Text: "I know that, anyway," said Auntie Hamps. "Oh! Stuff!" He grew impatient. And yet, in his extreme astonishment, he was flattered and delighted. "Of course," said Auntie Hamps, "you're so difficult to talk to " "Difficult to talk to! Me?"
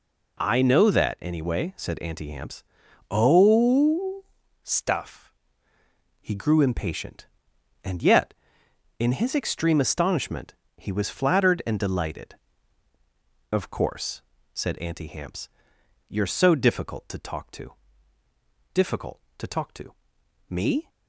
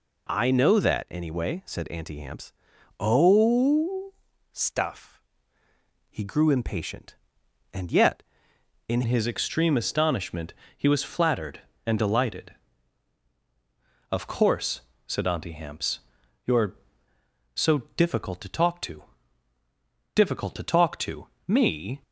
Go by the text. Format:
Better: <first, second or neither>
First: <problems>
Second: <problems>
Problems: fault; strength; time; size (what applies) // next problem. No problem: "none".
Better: first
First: none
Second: changes voice at "his"; from 9.0 s on; 13.0 s long // pauses between "so" and "difficult"; slight; at 17.7 s; 0.18 s long